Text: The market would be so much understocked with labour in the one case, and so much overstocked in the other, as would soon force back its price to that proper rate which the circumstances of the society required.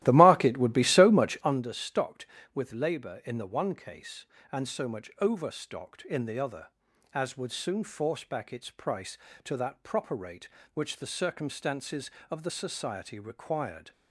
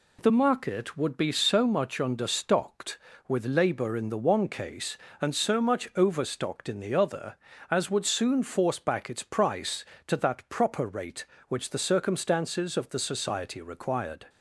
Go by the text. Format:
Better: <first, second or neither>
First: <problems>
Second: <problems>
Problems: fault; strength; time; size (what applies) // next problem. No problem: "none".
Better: second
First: starts louder than the rest; strong; until 1.6 s; 15 dB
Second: none